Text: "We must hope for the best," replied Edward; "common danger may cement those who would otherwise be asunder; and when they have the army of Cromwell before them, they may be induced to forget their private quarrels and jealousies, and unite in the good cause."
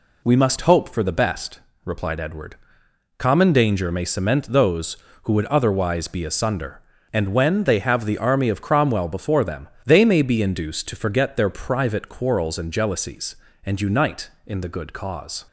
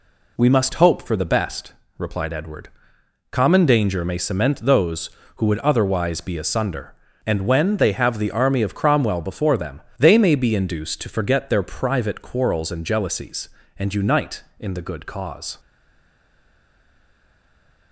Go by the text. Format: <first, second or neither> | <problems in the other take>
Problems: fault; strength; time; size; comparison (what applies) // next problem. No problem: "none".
first | stays silent after the last word; from 15.5 s on; 2.4 s long